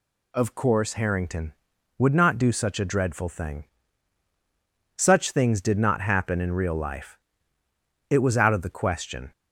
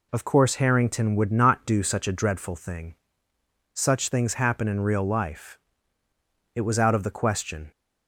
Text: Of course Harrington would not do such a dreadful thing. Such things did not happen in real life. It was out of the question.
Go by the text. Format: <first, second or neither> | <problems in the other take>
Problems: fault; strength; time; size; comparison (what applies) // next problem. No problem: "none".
first | skips "did not"; at 4.3 s